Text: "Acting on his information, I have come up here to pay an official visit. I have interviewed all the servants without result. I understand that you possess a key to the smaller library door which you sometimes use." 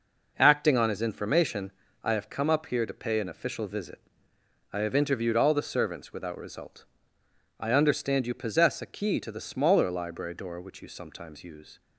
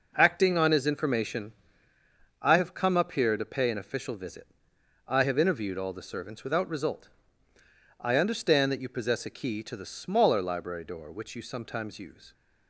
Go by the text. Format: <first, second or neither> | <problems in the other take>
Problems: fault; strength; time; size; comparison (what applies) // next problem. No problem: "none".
second | skips "that"; at 8.2 s